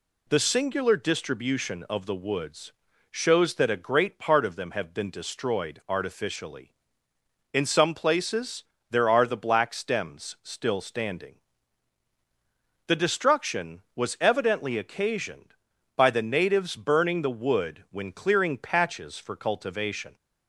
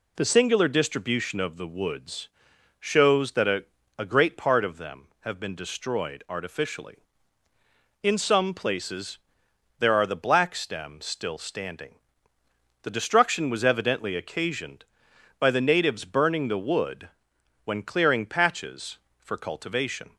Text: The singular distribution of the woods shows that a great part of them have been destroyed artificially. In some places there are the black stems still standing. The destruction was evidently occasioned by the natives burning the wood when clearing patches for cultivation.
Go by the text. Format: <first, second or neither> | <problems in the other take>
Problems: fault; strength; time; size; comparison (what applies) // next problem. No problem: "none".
first | pauses between "woods" and "shows"; noticeable; at 2.2 s; 0.50 s long; also in the first // says "a" twice; at 3.9 s // pauses between "places" and "there"; noticeable; at 9.1 s; 0.62 s long; slight in the first // pauses between "wood" and "when"; noticeable; at 17.0 s; 0.56 s long